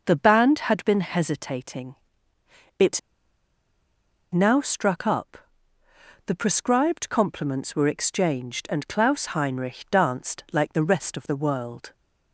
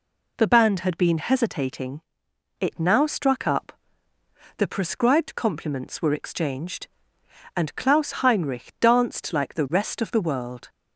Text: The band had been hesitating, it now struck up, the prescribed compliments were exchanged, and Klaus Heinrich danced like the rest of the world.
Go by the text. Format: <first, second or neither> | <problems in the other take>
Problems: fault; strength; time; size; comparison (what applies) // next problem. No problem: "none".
second | pauses between "it" and "now"; strong; at 2.9 s; 1.3 s long